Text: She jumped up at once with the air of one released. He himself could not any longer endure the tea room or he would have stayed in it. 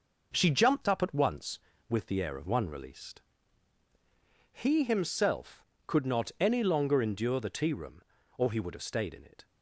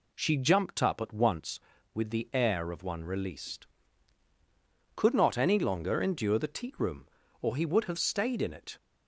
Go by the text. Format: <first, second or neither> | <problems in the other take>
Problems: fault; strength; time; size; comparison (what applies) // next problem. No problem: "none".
first | skips "He himself"; at 4.2 s